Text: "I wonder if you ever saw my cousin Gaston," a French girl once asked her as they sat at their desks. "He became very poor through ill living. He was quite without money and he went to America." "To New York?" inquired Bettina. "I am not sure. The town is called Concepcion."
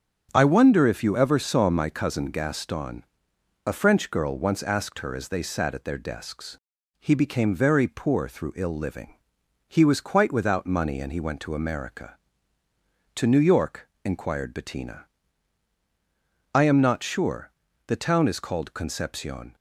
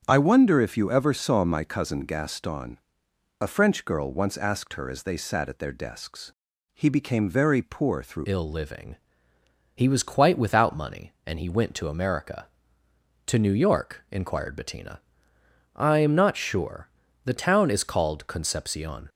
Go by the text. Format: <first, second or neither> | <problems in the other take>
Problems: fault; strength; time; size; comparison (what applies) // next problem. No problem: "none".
first | starts louder than the rest; strong; until 1.0 s; 8 dB; strong in the first // changes voice at "ill"; from 8.2 s on; 10.8 s long